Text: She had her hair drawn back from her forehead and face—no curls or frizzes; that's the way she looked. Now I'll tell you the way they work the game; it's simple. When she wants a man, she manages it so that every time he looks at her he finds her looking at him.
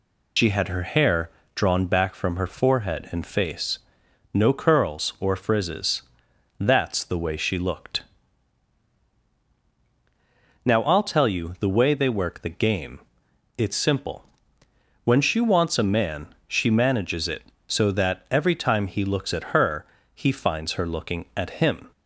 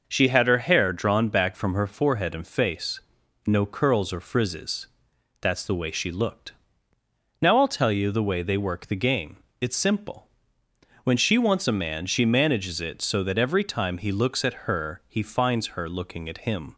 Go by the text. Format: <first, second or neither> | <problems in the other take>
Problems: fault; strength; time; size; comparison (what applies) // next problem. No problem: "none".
second | loses the start of "She"; at 0.3 s; 110 ms // pauses between "hair" and "drawn"; slight; at 1.2 s; 0.24 s long // pauses between "her" and "he"; slight; at 19.8 s; 0.30 s long